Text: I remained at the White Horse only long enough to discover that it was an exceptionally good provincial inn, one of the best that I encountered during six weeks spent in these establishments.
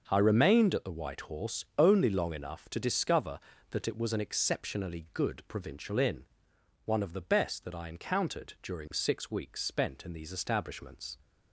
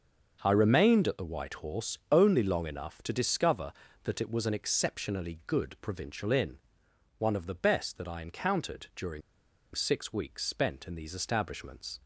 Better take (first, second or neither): first